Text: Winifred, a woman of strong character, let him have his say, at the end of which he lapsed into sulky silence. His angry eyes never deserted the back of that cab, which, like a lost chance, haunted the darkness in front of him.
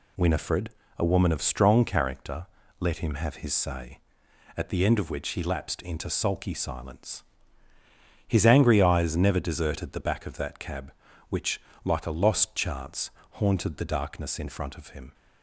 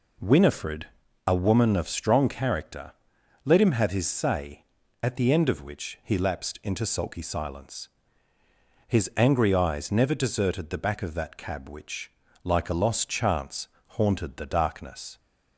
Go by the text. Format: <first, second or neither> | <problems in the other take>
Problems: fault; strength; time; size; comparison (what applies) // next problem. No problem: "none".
first | stops before "in front of him"; at 15.1 s